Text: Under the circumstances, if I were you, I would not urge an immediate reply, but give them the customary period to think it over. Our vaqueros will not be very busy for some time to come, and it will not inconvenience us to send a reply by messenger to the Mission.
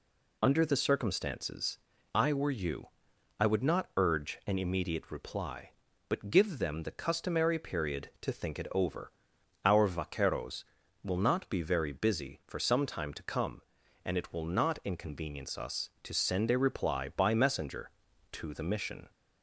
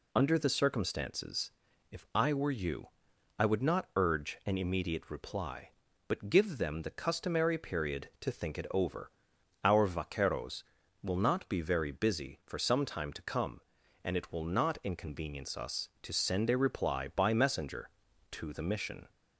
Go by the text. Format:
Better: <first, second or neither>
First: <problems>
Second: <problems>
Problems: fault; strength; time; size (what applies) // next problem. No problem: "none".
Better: second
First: skips "if"; at 1.9 s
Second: none